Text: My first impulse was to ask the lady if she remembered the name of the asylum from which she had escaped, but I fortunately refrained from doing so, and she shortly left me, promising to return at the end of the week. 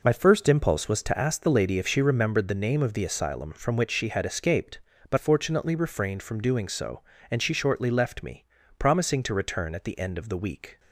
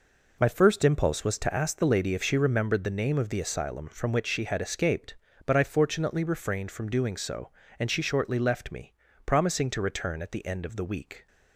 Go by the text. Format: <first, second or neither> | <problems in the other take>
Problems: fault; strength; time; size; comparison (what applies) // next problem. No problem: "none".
second | skips "I"; at 5.1 s